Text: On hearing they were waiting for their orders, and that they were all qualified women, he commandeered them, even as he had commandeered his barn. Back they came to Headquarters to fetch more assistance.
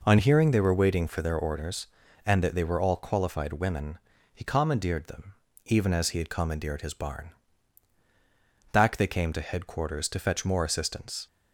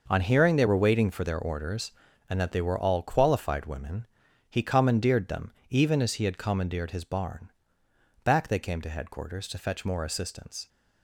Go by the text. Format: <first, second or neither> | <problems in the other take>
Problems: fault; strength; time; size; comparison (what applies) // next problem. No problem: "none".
neither | none